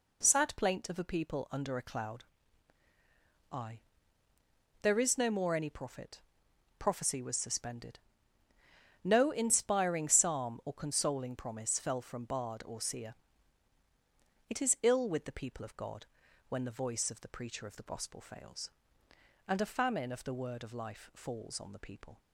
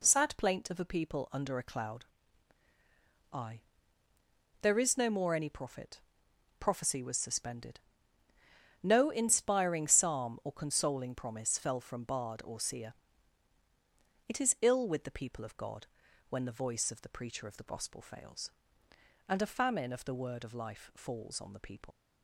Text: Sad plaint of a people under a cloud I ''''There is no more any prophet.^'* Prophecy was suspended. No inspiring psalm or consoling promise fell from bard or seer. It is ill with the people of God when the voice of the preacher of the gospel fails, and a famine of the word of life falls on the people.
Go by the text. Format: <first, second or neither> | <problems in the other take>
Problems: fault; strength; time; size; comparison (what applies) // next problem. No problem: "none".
first | pauses between "cloud" and "I"; strong; at 2.0 s; 1.2 s long; strong in the first // pauses between "I" and "There"; at 3.6 s; 1.0 s long; also in the first // pauses between "God" and "when"; at 15.8 s; 0.44 s long; also in the first // leaves "people" unfinished; at 21.9 s; 85 ms